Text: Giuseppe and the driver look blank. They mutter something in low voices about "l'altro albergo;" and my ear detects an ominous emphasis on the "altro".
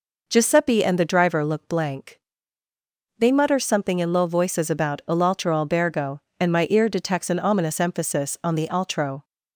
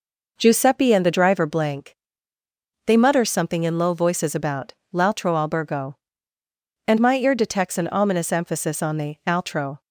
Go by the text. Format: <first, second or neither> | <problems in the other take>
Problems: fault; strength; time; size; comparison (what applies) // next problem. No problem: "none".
first | skips "look"; at 1.4 s // pauses between "about" and "l'altro"; slight; at 4.7 s; 0.18 s long